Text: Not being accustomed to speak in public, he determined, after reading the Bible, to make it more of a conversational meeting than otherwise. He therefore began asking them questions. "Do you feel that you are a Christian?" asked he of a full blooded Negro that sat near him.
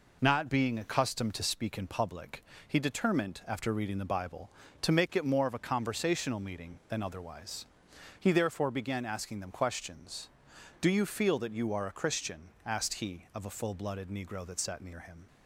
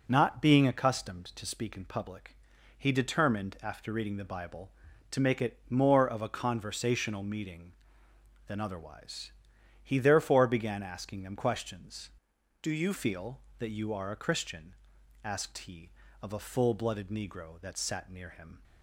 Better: first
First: none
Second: changes voice from "Do" to "you"; from 12.6 to 12.9 s; 0.3 s long

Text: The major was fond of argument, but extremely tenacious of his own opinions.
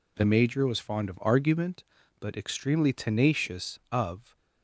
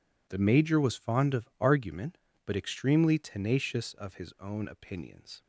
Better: second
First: stops before "his own opinions"; at 4.3 s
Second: none

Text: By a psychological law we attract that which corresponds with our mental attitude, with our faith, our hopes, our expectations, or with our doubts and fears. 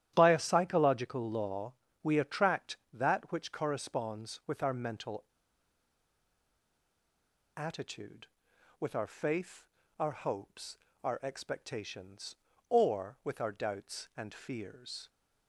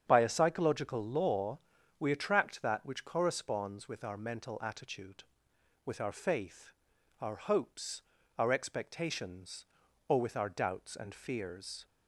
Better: second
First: starts louder than the rest; strong; until 1.1 s; 11.5 dB // pauses between "law" and "we"; slight; at 1.7 s; 0.32 s long // pauses between "mental" and "attitude"; strong; at 5.2 s; 2.3 s long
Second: starts louder than the rest; strong; until 1.0 s; 8 dB // pauses between "law" and "we"; at 1.5 s; 0.42 s long

